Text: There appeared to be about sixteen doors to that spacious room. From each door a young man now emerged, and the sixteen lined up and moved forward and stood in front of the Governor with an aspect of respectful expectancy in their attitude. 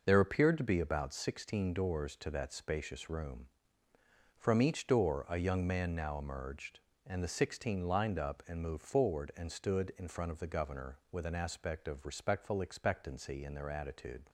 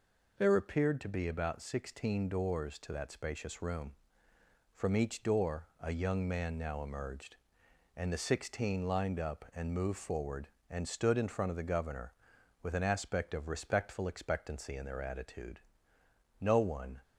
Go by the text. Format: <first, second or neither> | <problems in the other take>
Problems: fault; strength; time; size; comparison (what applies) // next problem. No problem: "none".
first | goes on to say "No one"; from 16.4 s on; 0.58 s long